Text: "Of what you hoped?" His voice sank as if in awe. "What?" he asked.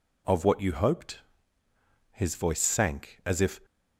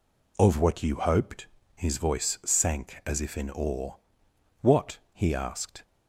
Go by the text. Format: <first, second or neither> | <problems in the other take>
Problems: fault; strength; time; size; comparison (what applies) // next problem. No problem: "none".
second | stops before "in awe What he asked"; at 3.6 s